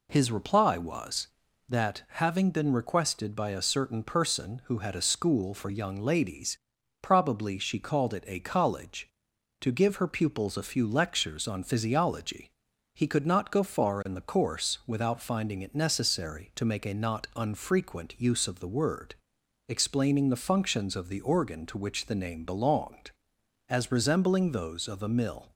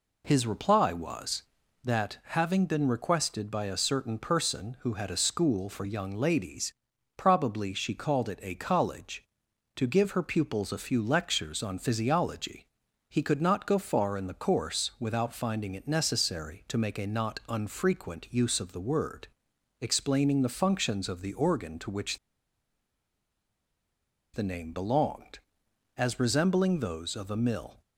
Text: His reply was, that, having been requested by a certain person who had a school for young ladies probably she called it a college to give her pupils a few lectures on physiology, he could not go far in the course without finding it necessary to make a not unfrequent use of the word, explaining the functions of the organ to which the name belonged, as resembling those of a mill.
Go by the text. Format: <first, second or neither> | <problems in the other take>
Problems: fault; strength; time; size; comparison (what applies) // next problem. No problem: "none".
first | pauses between "ladies" and "probably"; at 6.7 s; 0.44 s long; also in the first // pauses between "which" and "the"; strong; at 22.1 s; 2.1 s long